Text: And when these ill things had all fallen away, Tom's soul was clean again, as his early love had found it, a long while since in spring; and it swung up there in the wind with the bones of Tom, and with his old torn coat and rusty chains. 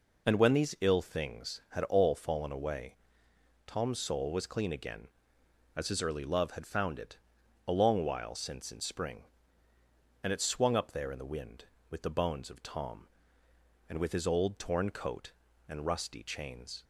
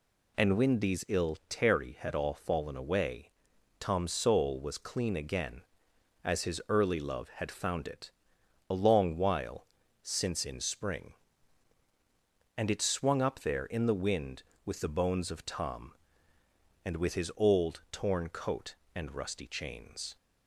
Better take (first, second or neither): first